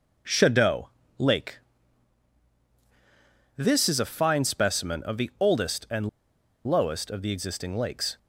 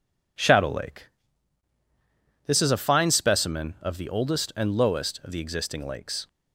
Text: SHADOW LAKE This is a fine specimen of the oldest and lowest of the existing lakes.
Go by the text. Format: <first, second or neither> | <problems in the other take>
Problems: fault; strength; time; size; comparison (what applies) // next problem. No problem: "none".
second | pauses between "SHADOW" and "LAKE"; slight; at 0.8 s; 0.30 s long // pauses between "LAKE" and "This"; strong; at 1.5 s; 1.9 s long; strong in the second // pauses between "and" and "lowest"; noticeable; at 6.0 s; 0.58 s long